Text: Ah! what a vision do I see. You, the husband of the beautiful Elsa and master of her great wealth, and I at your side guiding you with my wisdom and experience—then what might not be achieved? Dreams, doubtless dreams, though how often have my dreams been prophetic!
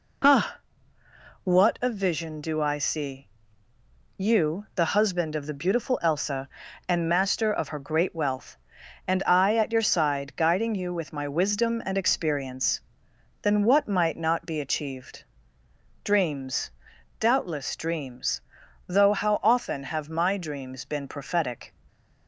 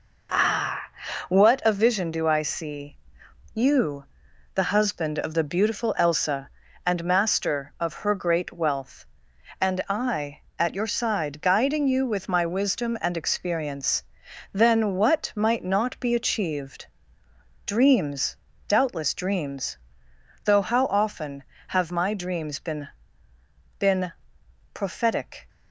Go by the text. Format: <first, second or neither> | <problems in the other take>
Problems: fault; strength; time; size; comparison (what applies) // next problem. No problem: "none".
first | says "been" twice; at 23.7 s